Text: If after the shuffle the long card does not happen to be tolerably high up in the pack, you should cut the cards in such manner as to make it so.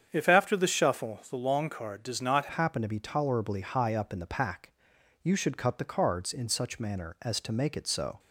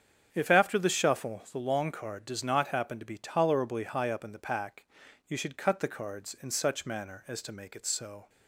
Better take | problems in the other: second | starts louder than the rest; strong; until 1.1 s; 8 dB; strong in the second // changes voice at "happen"; from 2.5 s on; 5.6 s long

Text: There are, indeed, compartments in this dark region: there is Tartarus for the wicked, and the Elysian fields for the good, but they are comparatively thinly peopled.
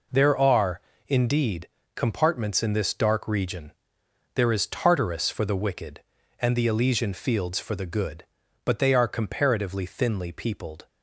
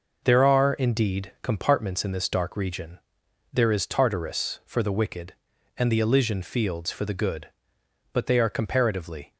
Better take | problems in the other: first | stops before "thinly peopled"; at 9.3 s

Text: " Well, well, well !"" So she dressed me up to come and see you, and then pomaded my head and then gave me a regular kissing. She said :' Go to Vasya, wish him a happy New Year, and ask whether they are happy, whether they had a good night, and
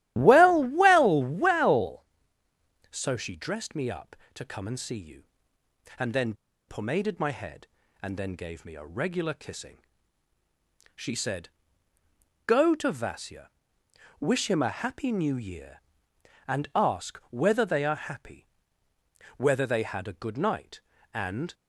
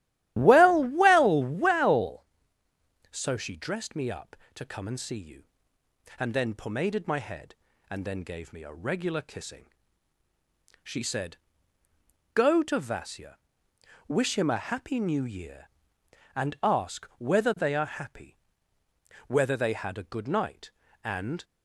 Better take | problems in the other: second | starts louder than the rest; strong; until 1.1 s; 16.5 dB; strong in the second // pauses between "then" and "pomaded"; slight; at 6.3 s; 0.35 s long

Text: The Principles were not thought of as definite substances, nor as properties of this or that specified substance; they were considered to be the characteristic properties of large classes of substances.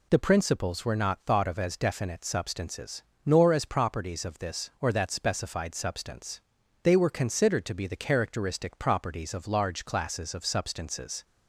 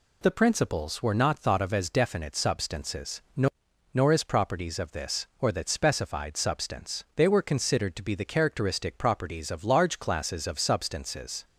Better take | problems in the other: first | says "nor" twice; at 3.9 s

